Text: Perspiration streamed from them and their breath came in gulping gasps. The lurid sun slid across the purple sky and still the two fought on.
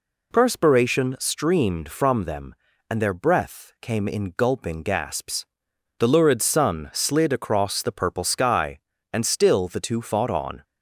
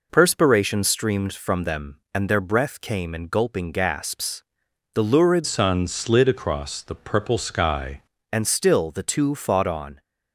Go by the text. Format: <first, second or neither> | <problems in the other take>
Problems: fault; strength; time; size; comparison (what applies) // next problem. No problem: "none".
first | changes voice from "sun" to "sky"; from 5.4 to 8.0 s; 2.6 s long